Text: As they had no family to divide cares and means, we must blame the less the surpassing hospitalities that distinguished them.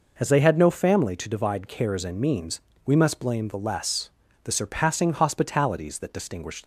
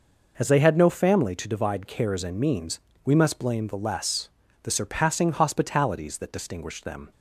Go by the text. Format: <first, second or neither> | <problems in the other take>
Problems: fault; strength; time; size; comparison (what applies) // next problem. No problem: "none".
second | pauses between "less" and "the"; slight; at 4.0 s; 0.34 s long; slight in the second // stops before "them"; at 6.6 s